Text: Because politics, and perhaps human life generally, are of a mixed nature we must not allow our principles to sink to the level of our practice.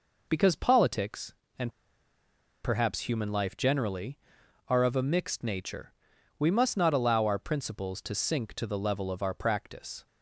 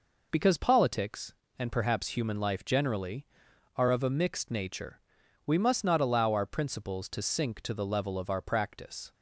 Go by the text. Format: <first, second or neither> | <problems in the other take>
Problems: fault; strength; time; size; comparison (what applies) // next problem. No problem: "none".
second | pauses between "and" and "perhaps"; noticeable; at 1.7 s; 0.92 s long // pauses between "nature" and "we"; noticeable; at 5.9 s; 0.46 s long; noticeable in the second